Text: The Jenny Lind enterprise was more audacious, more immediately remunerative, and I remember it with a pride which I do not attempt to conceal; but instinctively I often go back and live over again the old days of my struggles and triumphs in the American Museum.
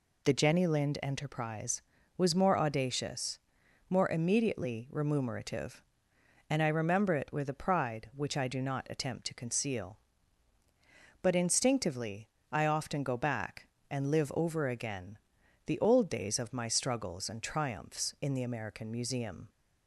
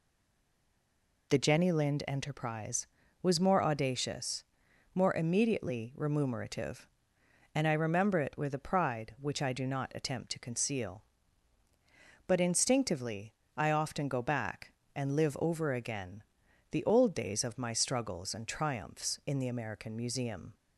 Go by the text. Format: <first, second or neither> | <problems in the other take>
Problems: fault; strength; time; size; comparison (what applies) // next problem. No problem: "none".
first | stays silent before the first word; noticeable; until 1.2 s; 1.2 s long // pauses between "instinctively" and "I"; slight; at 13.3 s; 0.22 s long; slight in the first // pauses between "again" and "the"; noticeable; at 16.2 s; 0.48 s long; noticeable in the first